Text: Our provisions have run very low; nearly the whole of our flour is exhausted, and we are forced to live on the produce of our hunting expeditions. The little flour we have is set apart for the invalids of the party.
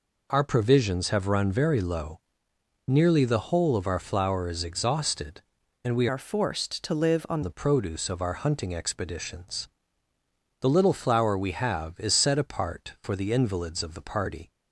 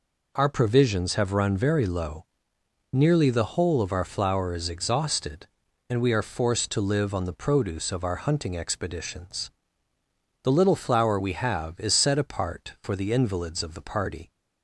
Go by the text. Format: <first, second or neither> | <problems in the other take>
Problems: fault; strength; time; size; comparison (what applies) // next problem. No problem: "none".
second | changes voice from "are" to "on"; from 6.0 to 7.4 s; 1.4 s long